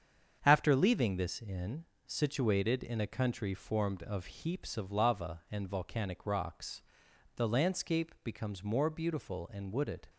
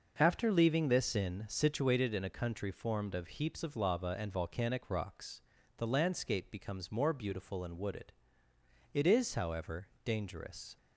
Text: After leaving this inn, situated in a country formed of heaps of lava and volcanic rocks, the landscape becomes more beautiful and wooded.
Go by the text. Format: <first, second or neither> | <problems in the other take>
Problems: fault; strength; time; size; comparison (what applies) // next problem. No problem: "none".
first | starts louder than the rest; noticeable; until 1.1 s; 6 dB; strong in the first // goes on to say "It is however dangerous"; strong; from 8.9 s on; 1.8 s long